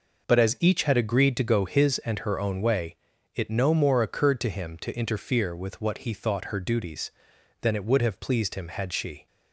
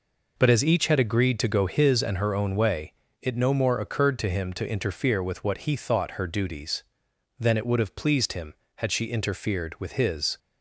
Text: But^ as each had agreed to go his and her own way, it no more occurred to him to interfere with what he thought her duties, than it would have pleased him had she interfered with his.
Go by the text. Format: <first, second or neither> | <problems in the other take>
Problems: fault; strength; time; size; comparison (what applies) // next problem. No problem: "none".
second | stops before "interfered with his"; at 9.2 s